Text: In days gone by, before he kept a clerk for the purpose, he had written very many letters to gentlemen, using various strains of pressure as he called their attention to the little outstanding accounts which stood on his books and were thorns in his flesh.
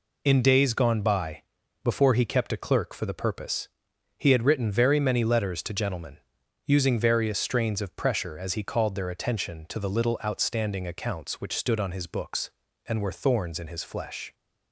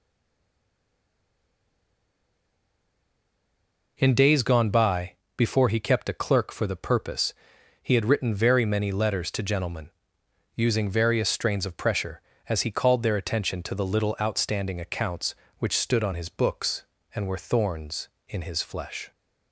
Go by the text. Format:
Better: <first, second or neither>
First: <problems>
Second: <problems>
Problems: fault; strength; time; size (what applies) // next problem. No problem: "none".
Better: first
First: none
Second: stays silent before the first word; strong; until 3.9 s; 3.9 s long